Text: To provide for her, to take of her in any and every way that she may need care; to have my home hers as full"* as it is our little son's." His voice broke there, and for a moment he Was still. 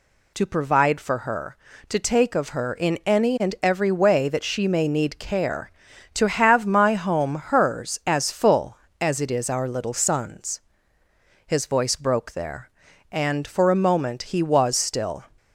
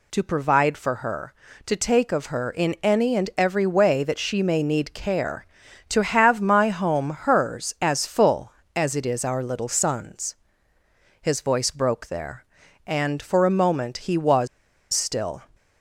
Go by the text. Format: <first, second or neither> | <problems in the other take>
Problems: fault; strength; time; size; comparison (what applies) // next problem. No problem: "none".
first | pauses between "Was" and "still"; noticeable; at 14.4 s; 0.46 s long